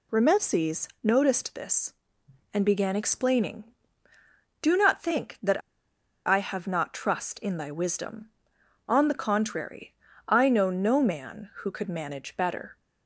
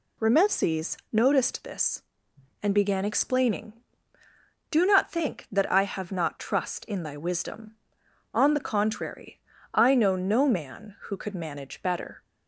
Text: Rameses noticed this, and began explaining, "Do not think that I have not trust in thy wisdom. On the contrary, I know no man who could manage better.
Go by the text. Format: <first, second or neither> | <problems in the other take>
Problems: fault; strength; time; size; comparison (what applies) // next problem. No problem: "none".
second | pauses between "Rameses" and "noticed"; slight; at 0.8 s; 0.16 s long; slight in the second // pauses between "that" and "I"; noticeable; at 5.6 s; 0.65 s long